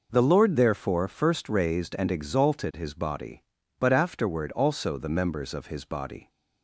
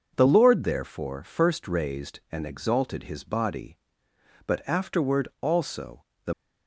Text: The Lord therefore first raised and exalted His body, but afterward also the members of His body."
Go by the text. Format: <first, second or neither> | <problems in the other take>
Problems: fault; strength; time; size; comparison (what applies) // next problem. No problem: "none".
first | pauses between "also" and "the"; slight; at 6.0 s; 0.22 s long // stops before "members of His body"; at 6.3 s